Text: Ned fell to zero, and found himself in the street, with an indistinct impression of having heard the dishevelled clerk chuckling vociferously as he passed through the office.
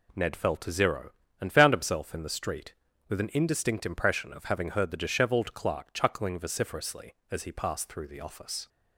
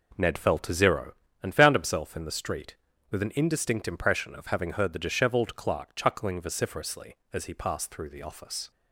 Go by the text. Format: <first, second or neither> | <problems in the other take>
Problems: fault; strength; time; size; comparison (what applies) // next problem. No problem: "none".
first | starts louder than the rest; noticeable; until 1.2 s; 4.5 dB